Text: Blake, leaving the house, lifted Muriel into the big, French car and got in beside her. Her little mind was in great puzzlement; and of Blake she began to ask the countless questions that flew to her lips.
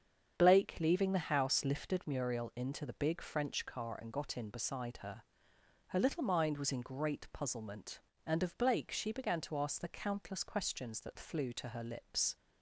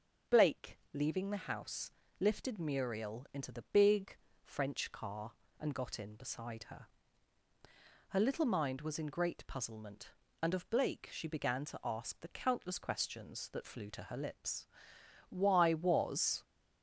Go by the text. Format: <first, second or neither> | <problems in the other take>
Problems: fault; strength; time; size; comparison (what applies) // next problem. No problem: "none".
first | starts louder than the rest; until 1.4 s; 6.5 dB; strong in the first // goes on to say "Why was"; noticeable; from 15.2 s on; 1.1 s long